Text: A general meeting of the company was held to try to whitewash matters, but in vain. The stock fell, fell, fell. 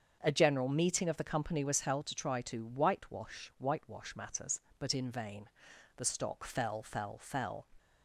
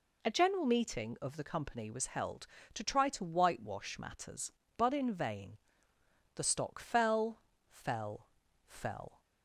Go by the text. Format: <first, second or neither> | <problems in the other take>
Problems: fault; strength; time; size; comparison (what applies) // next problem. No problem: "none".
second | starts louder than the rest; until 1.2 s; 7 dB // says "whitewash" twice; at 3.5 s